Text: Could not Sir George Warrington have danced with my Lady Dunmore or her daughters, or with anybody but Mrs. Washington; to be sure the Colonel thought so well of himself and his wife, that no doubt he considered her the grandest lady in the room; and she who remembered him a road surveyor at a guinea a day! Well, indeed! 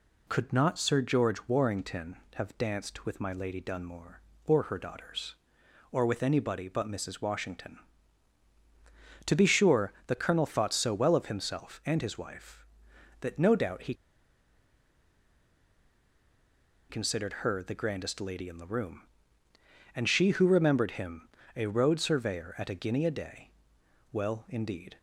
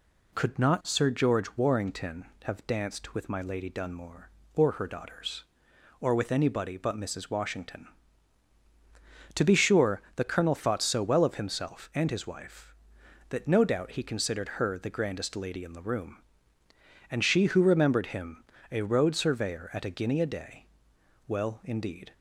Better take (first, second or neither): second